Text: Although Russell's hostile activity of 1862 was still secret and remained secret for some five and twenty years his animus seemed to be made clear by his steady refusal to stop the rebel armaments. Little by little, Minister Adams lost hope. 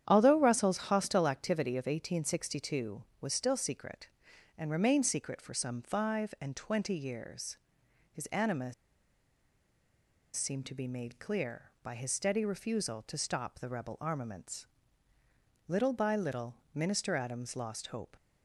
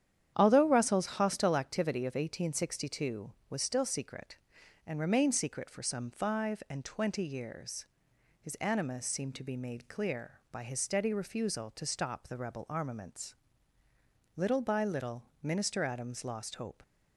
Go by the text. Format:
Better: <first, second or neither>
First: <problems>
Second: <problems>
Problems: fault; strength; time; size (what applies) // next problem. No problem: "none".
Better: second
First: starts louder than the rest; strong; until 1.0 s; 9.5 dB // pauses between "years" and "his"; noticeable; at 7.5 s; 0.54 s long // pauses between "animus" and "seemed"; strong; at 8.7 s; 1.6 s long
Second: starts louder than the rest; strong; until 1.3 s; 9.5 dB // pauses between "years" and "his"; noticeable; at 7.8 s; 0.54 s long